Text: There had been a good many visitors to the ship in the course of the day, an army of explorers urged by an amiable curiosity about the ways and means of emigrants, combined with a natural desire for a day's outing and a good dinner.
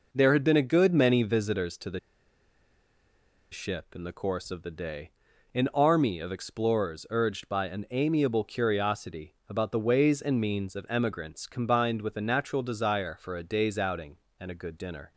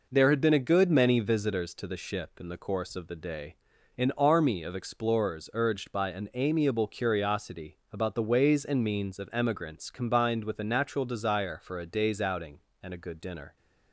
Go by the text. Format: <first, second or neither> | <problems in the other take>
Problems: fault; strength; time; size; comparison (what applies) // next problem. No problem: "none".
second | pauses between "the" and "ship"; strong; at 1.9 s; 1.5 s long